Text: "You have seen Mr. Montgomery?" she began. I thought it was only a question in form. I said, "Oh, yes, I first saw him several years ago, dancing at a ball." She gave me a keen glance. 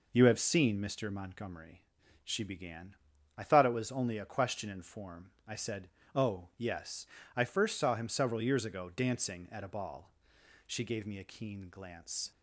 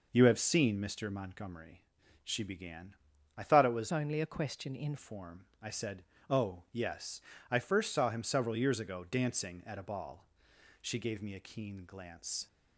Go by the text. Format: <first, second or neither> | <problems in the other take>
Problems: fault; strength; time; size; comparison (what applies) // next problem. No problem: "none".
first | changes voice from "only" to "in"; from 3.9 to 4.9 s; 1.0 s long